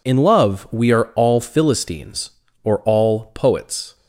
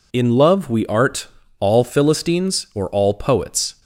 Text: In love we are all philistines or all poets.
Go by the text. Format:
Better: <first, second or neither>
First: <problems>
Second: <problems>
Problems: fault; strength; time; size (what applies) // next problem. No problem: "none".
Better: first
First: none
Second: says "art" for "are"; at 0.8 s